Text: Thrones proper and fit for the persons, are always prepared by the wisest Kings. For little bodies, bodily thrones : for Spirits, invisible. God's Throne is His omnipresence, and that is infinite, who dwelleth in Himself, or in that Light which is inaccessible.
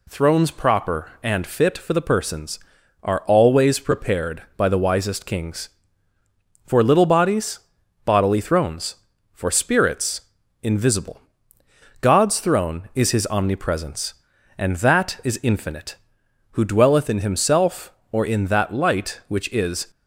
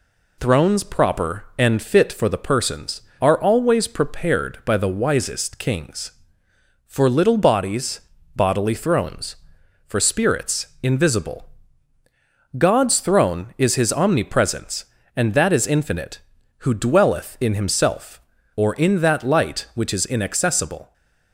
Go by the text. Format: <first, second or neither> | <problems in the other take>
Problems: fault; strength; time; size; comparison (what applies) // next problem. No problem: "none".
second | stops before "inaccessible"; at 19.9 s